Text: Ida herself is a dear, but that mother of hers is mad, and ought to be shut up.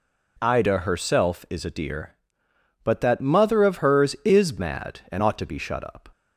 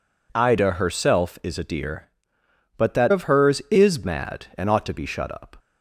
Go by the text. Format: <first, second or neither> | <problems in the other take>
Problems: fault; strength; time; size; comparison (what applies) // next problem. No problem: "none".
first | skips "mother"; at 3.1 s